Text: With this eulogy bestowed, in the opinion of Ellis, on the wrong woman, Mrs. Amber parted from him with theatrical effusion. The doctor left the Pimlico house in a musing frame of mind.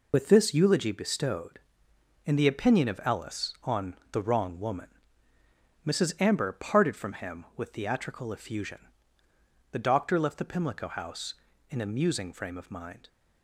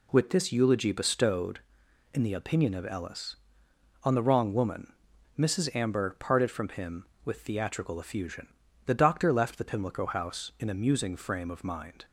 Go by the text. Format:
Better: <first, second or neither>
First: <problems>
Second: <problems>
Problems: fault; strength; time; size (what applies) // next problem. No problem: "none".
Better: second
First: loses the start of "With"; at 0.1 s; 45 ms // pauses between "on" and "the"; slight; at 3.9 s; 0.20 s long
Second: none